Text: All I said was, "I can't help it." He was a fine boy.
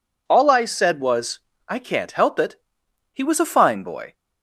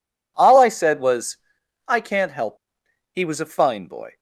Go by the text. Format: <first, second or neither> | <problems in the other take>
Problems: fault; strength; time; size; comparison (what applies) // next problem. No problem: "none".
first | skips "it"; at 2.8 s